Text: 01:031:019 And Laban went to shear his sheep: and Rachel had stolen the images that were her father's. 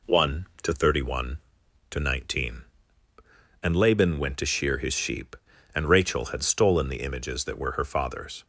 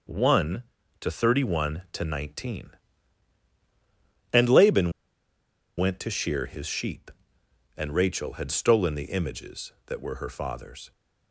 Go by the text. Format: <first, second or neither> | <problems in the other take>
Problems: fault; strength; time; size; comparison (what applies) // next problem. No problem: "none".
first | pauses between "Laban" and "went"; noticeable; at 4.8 s; 0.87 s long